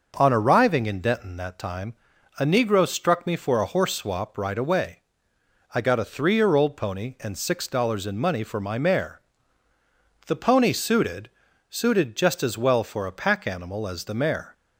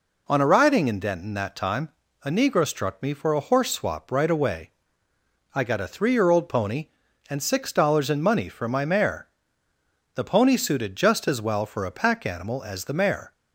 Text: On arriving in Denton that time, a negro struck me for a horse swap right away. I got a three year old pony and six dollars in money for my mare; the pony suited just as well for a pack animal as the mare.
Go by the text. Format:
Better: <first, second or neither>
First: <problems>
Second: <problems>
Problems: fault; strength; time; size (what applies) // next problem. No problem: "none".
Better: second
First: starts louder than the rest; noticeable; until 1.1 s; 6 dB // says "suited" twice; at 11.6 s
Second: none